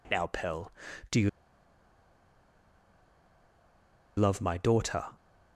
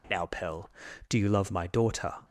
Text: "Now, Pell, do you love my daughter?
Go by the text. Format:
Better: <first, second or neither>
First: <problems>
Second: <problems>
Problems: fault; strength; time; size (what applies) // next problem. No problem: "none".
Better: second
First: pauses between "you" and "love"; strong; at 1.2 s; 2.8 s long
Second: none